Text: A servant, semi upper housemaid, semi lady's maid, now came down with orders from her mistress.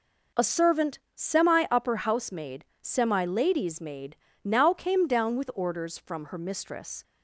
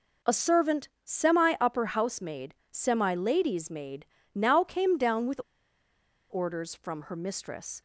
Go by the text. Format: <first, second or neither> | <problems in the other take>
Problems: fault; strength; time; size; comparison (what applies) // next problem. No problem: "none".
first | pauses between "with" and "orders"; noticeable; at 5.4 s; 0.90 s long